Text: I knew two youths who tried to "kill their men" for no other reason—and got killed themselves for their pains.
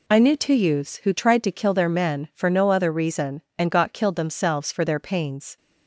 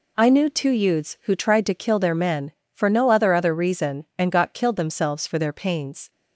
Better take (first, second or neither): first